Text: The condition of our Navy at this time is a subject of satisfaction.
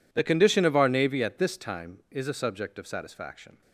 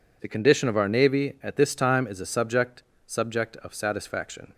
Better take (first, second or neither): first